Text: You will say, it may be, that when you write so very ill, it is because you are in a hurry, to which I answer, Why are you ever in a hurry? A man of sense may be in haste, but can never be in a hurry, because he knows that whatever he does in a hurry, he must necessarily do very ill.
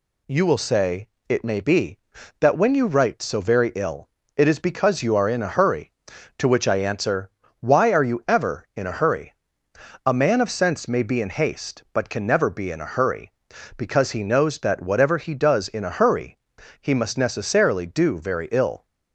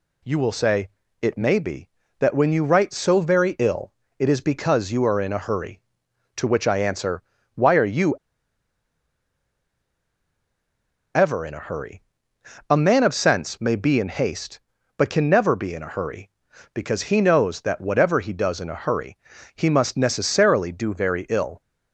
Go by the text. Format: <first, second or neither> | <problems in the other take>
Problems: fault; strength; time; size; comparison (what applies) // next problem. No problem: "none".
first | pauses between "you" and "ever"; strong; at 8.1 s; 3.0 s long